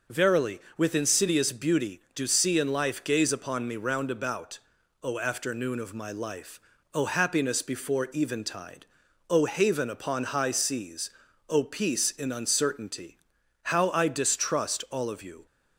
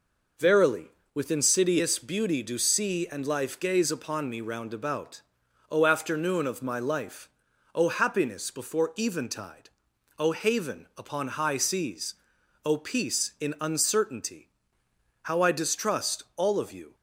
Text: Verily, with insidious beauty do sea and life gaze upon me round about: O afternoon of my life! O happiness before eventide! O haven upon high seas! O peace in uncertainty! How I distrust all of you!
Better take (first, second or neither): neither